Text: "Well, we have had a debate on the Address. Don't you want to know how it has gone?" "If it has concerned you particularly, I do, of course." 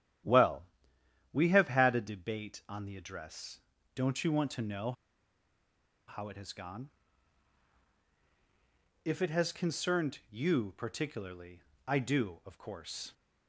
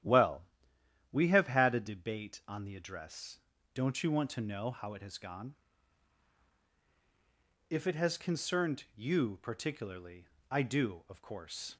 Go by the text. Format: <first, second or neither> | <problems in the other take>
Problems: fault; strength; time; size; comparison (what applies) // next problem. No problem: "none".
second | starts louder than the rest; strong; until 1.9 s; 11.5 dB; strong in the second // pauses between "know" and "how"; at 4.9 s; 1.1 s long